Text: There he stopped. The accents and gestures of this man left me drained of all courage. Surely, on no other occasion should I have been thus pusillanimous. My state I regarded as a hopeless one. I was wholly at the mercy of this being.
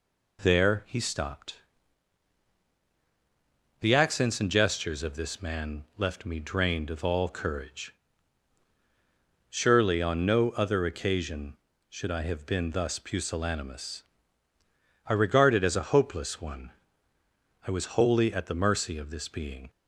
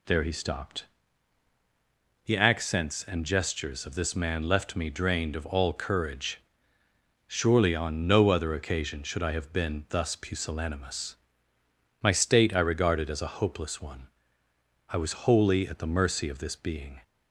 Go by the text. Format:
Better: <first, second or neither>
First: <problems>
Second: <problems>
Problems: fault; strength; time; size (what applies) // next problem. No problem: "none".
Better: second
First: skips "My state"; at 14.5 s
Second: none